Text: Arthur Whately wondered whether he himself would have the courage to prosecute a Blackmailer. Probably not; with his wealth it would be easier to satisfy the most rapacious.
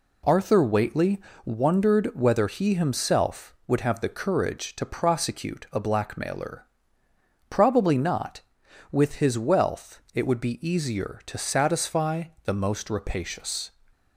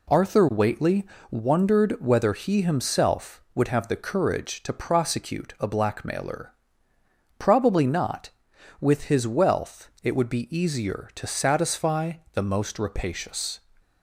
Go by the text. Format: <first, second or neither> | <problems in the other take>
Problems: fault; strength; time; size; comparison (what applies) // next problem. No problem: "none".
neither | pauses between "Whately" and "wondered"; slight; the same in both // pauses between "satisfy" and "the"; slight; the same in both